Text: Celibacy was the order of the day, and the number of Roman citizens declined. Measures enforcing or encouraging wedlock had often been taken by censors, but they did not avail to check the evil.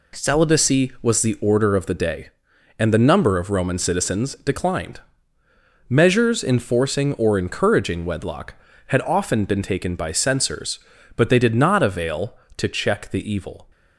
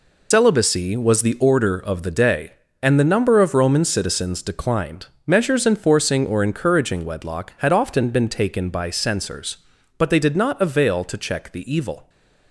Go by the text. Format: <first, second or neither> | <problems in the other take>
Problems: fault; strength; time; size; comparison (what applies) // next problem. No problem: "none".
first | loses the start of "Celibacy"; at 0.3 s; 115 ms